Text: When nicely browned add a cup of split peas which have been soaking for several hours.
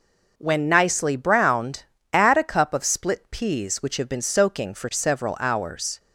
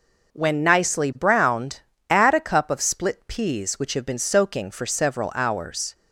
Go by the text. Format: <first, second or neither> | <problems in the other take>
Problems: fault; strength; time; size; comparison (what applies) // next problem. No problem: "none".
neither | pauses between "browned" and "add"; slight; the same in both